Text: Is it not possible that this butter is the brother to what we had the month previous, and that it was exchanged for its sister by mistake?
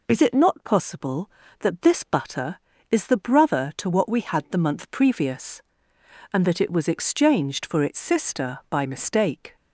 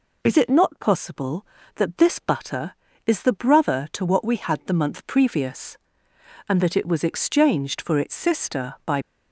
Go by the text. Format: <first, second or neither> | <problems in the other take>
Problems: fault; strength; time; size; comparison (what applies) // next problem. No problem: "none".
first | stops before "mistake"; at 9.0 s